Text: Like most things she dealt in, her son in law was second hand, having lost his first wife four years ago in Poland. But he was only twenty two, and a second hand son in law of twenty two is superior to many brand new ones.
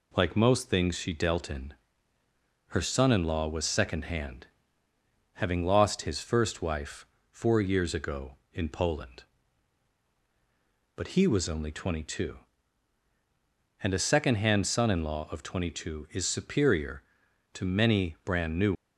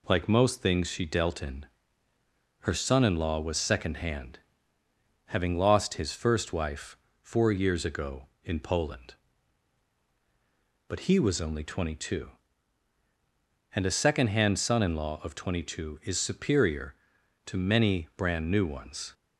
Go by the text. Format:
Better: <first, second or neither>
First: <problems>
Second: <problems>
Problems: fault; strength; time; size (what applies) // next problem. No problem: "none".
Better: second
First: pauses between "wife" and "four"; slight; at 7.0 s; 0.24 s long // stops before "ones"; at 18.7 s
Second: pauses between "wife" and "four"; slight; at 6.9 s; 0.24 s long